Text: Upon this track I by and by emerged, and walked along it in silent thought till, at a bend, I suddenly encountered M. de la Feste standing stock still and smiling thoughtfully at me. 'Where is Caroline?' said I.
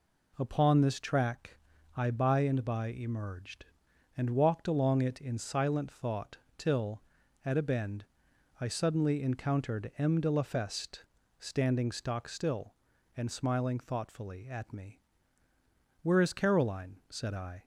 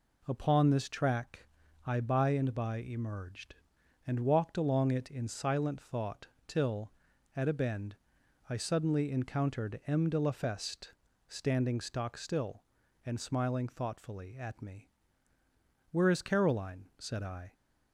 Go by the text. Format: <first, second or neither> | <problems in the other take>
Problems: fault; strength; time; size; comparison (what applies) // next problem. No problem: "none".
neither | pauses between "track" and "I"; the same in both // pauses between "thought" and "till"; slight; the same in both // pauses between "Feste" and "standing"; slight; the same in both